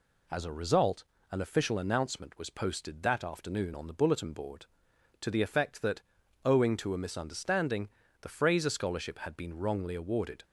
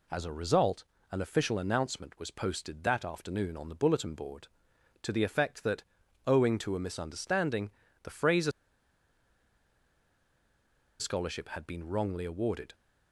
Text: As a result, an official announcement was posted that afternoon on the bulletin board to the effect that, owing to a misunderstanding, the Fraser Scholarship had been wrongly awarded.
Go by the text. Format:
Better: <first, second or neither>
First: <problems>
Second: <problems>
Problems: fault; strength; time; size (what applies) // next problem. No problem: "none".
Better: first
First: none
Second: pauses between "Fraser" and "Scholarship"; strong; at 8.5 s; 2.4 s long